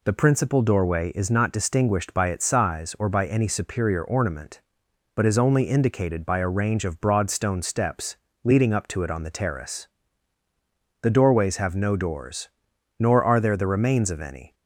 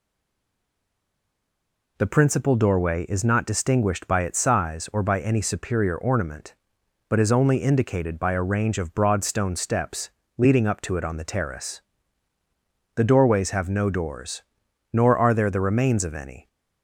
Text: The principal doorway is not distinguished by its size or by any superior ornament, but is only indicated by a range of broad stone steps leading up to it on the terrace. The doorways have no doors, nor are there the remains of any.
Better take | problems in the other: first | stays silent before the first word; noticeable; until 1.9 s; 1.9 s long // pauses between "steps" and "leading"; slight; at 10.0 s; 0.26 s long; slight in the first

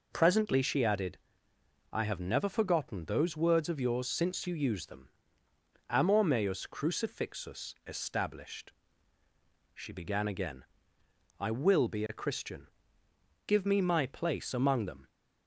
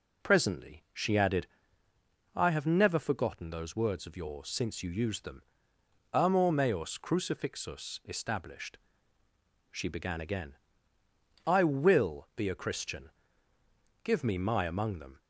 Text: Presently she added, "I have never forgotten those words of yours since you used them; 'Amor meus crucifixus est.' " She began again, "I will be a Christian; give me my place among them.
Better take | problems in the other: first | skips "place"; at 14.6 s

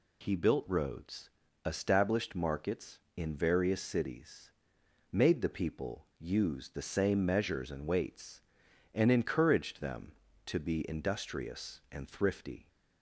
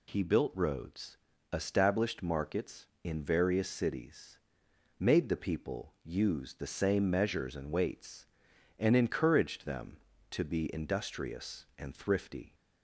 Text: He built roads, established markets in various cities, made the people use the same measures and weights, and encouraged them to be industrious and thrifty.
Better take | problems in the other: neither | none

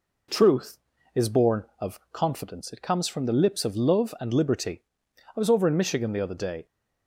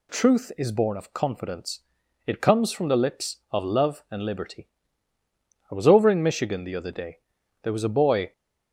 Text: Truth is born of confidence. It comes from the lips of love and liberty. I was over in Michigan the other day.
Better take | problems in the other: first | goes on to say "There was a boy"; noticeable; from 7.6 s on; 0.70 s long

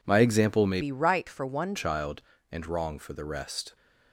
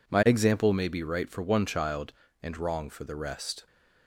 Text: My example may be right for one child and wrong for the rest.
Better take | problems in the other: second | changes voice from "be" to "one"; from 0.8 to 1.7 s; 0.9 s long

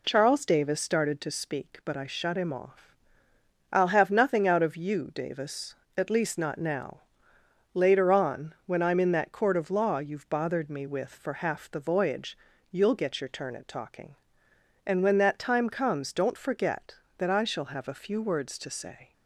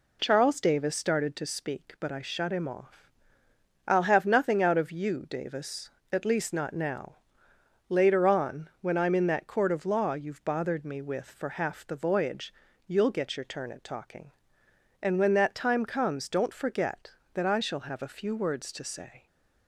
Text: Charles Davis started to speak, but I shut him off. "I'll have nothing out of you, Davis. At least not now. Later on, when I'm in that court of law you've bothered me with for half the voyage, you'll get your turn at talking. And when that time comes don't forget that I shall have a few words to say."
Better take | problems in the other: neither | none

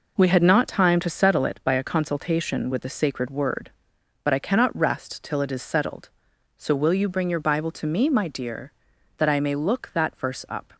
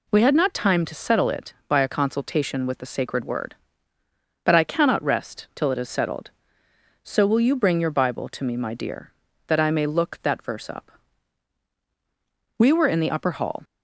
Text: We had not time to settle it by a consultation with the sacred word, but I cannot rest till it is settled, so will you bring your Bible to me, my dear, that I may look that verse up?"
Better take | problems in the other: first | goes on to say "We were in the upper hall"; noticeable; from 12.5 s on; 1.0 s long

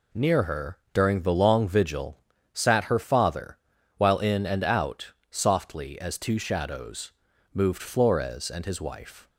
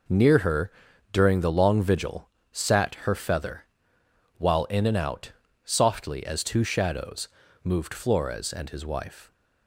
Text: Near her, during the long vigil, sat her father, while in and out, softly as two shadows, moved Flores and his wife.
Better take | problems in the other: first | says "feather" for "father"; at 3.1 s

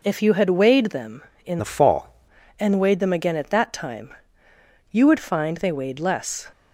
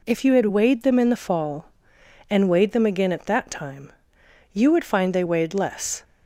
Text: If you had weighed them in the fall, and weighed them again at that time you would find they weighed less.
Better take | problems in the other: second | changes voice from "the" to "fall"; from 1.5 to 2.0 s; 0.5 s long // pauses between "time" and "you"; noticeable; at 4.1 s; 0.78 s long; noticeable in the second

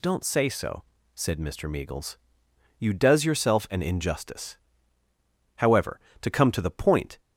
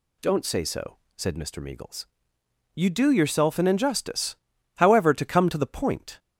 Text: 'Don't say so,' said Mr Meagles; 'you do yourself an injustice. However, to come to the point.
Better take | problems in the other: second | says "does" for "do"; at 2.9 s

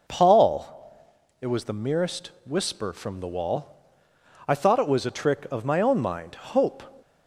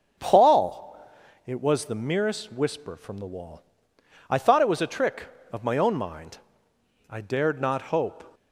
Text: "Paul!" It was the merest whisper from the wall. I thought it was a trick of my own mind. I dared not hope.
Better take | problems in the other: second | pauses between "merest" and "whisper"; slight; at 2.2 s; 0.16 s long // skips "I dared not"; at 6.3 s

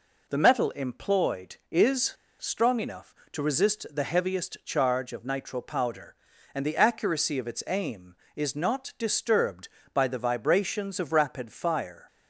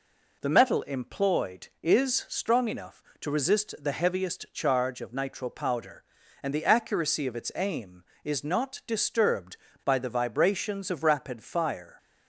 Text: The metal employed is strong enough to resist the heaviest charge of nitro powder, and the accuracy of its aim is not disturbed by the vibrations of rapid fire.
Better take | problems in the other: second | pauses between "is" and "strong"; slight; at 2.1 s; 0.25 s long

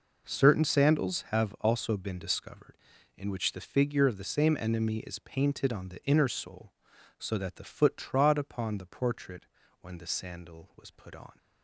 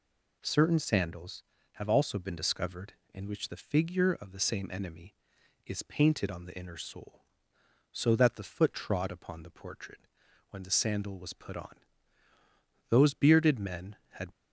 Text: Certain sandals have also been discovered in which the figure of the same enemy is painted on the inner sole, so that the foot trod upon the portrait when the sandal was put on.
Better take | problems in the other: first | pauses between "portrait" and "when"; noticeable; at 9.9 s; 0.50 s long; slight in the first // goes on to say "Those bearded men had"; from 12.8 s on; 1.4 s long

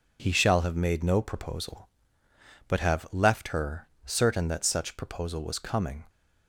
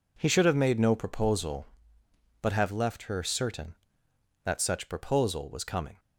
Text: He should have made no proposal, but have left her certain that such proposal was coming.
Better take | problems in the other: second | says "shall" for "should"; at 0.3 s // pauses between "her" and "certain"; slight; at 3.8 s; 0.18 s long

